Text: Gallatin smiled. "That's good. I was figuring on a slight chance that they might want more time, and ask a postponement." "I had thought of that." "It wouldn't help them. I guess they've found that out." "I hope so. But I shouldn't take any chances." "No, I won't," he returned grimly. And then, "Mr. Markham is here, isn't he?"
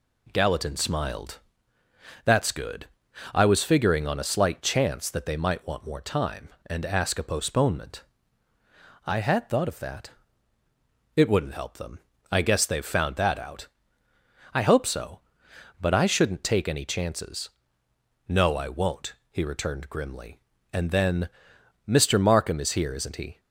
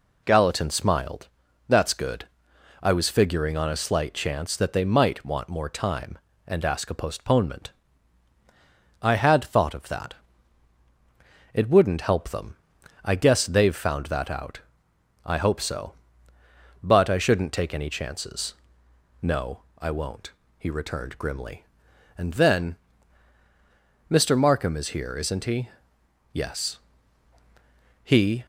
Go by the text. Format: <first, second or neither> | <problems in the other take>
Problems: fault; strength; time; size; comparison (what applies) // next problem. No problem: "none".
first | goes on to say "Yes He"; strong; from 26.3 s on; 2.1 s long